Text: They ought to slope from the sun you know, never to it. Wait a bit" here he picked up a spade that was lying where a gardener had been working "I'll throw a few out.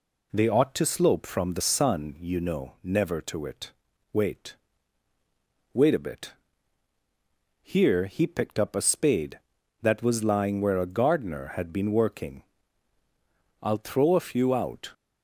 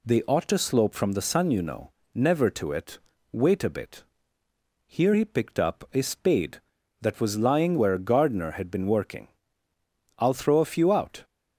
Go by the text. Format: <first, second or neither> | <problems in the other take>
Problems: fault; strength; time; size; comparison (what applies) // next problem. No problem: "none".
second | says "Wait" twice; at 5.7 s // pauses between "bit" and "here"; strong; at 6.3 s; 1.3 s long; noticeable in the second // pauses between "working" and "I'll"; at 12.4 s; 1.2 s long; noticeable in the second